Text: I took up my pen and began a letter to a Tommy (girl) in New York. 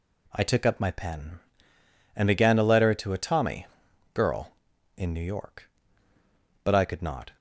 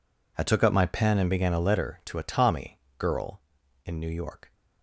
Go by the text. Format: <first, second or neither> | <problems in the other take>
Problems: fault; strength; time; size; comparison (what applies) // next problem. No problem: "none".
second | goes on to say "But I could not"; noticeable; from 6.6 s on; 0.74 s long